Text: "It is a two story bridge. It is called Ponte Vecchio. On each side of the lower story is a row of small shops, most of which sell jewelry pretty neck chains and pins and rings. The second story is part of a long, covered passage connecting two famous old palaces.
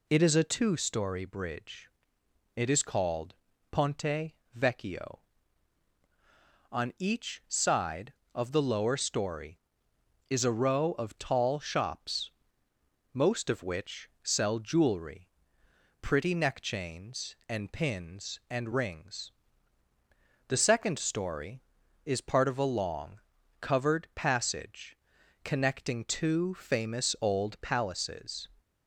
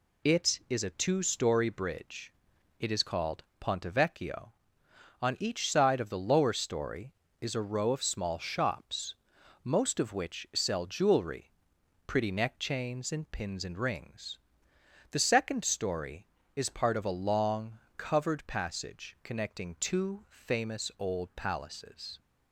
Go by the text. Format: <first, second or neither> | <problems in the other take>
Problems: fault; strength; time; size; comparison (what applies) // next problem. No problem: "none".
second | pauses between "called" and "Ponte"; at 3.3 s; 0.38 s long // pauses between "Ponte" and "Vecchio"; slight; at 4.3 s; 0.23 s long // says "tall" for "small"; at 11.1 s // pauses between "jewelry" and "pretty"; noticeable; at 15.2 s; 0.72 s long; noticeable in the second // pauses between "passage" and "connecting"; noticeable; at 24.9 s; 0.46 s long